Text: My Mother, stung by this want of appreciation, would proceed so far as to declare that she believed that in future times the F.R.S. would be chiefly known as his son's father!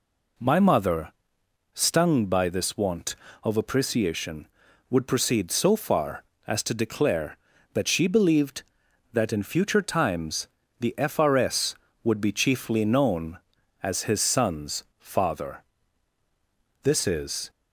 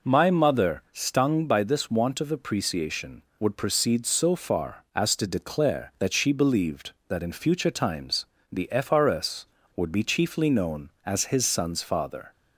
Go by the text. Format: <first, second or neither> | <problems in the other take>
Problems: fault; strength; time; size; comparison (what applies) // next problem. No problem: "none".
second | pauses between "times" and "the"; slight; at 10.4 s; 0.32 s long; slight in the second // goes on to say "This is"; noticeable; from 16.8 s on; 0.66 s long